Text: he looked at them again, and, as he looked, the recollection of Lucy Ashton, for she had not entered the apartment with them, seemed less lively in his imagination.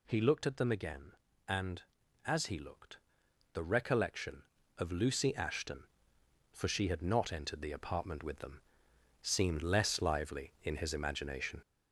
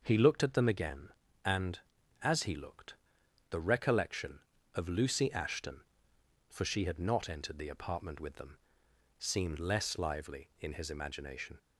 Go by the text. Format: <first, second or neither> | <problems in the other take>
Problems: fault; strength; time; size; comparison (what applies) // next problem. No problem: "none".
second | gets louder; noticeable; throughout; 4.5 dB